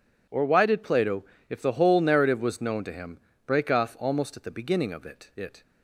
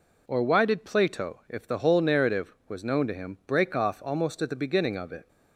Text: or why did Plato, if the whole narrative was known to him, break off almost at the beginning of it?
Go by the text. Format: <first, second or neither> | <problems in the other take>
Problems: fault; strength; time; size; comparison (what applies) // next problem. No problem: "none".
second | says "it" twice; at 5.3 s